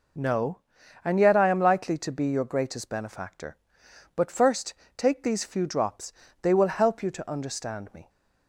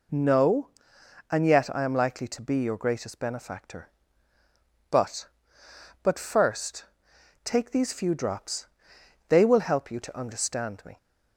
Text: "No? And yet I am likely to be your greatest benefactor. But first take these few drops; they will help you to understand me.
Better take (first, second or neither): first